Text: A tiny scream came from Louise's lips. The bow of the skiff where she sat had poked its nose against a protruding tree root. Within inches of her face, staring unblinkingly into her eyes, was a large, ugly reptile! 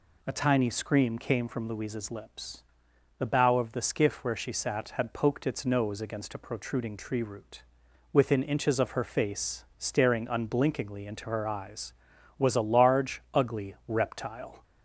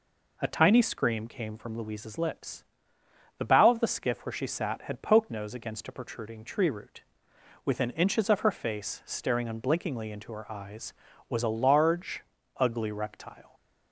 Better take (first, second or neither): first